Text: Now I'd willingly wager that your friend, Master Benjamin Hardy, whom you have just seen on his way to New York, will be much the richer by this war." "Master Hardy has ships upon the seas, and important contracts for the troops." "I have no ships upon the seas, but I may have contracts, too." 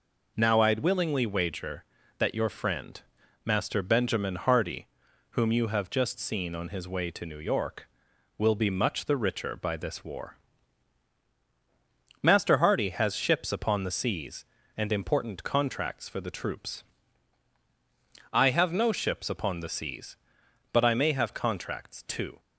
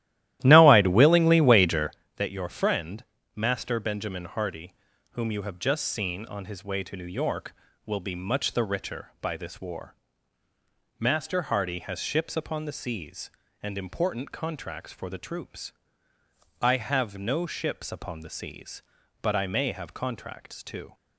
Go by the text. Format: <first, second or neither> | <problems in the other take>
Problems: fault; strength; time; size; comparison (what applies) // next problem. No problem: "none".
first | starts louder than the rest; strong; until 2.0 s; 14 dB